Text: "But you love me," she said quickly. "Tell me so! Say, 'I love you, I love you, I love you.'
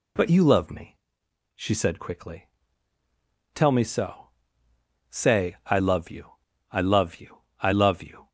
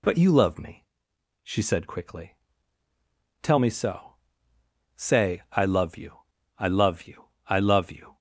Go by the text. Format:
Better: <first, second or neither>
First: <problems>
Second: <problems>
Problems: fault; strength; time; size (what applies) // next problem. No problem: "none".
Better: neither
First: none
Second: none